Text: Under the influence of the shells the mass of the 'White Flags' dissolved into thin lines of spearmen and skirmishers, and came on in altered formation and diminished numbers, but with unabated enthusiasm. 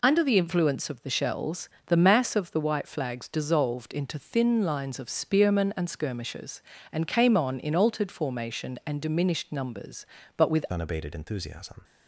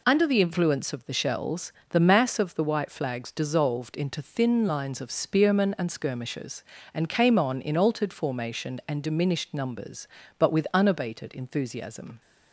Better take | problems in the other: second | pauses between "shells" and "the"; slight; at 1.6 s; 0.18 s long; slight in the second // changes voice at "unabated"; from 10.7 s on; 1.1 s long

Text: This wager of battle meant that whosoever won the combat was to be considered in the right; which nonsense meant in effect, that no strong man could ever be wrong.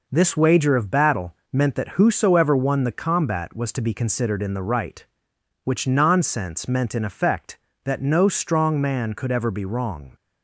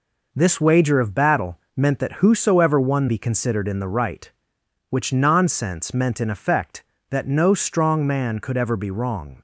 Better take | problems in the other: first | pauses between "battle" and "meant"; slight; at 1.5 s; 0.18 s long; slight in the first // skips "the combat was to"; at 3.0 s

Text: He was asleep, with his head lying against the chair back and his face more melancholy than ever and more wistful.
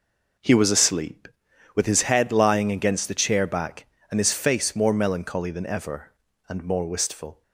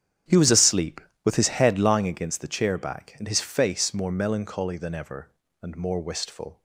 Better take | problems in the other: first | starts louder than the rest; strong; until 2.2 s; 9 dB

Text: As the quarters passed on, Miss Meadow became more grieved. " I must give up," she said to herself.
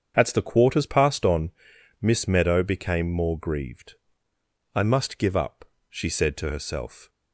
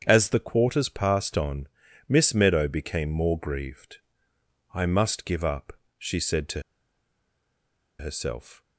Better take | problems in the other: first | starts louder than the rest; strong; until 1.0 s; 8 dB; strong in the first // pauses between "to" and "herself"; strong; at 6.6 s; 1.3 s long

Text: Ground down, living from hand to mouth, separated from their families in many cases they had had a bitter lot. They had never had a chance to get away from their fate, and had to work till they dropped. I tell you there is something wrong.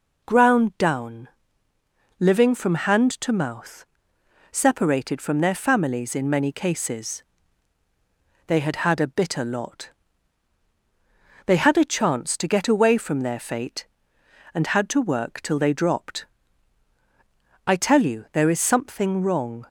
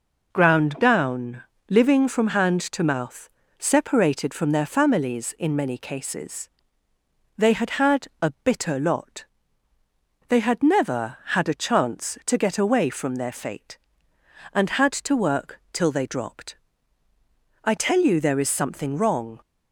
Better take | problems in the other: second | pauses between "cases" and "they"; at 7.2 s; 1.2 s long; noticeable in the second // skips "never had"; at 11.7 s

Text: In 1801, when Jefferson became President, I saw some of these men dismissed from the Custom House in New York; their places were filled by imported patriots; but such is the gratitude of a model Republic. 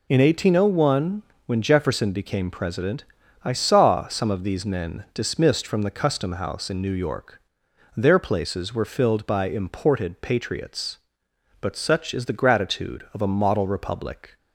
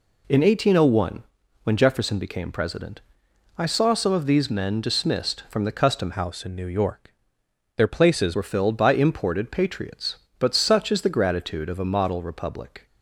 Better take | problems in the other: first | changes voice from "House" to "places"; from 6.1 to 8.3 s; 2.2 s long

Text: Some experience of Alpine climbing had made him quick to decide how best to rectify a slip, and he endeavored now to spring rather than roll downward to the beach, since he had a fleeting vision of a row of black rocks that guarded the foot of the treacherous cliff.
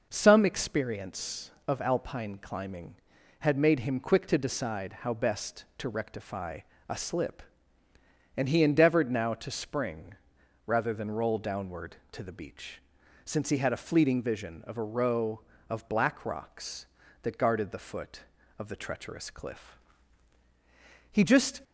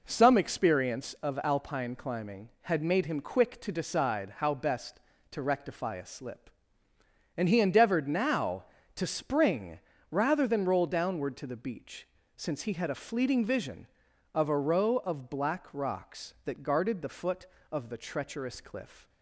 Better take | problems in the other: second | pauses between "rectify" and "a"; slight; at 6.6 s; 0.28 s long // pauses between "spring" and "rather"; noticeable; at 10.1 s; 0.52 s long; slight in the second // goes on to say "He just"; slight; from 21.1 s on; 0.48 s long

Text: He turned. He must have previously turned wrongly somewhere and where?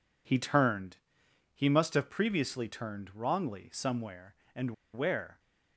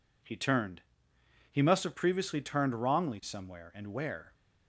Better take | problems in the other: second | pauses between "and" and "where"; slight; at 4.7 s; 0.21 s long

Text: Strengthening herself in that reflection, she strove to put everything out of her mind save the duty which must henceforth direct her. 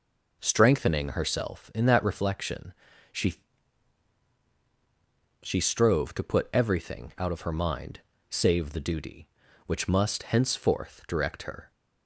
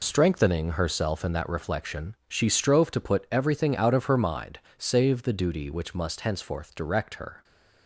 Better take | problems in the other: second | says "she" twice; at 5.4 s // pauses between "mind" and "save"; slight; at 7.9 s; 0.28 s long; slight in the second

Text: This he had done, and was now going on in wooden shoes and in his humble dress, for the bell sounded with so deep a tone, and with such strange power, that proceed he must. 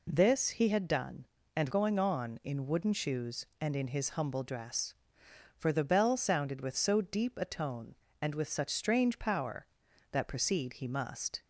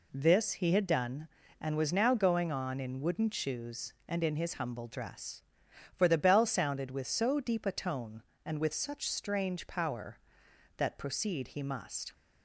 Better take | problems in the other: second | skips "was now"; at 1.6 s

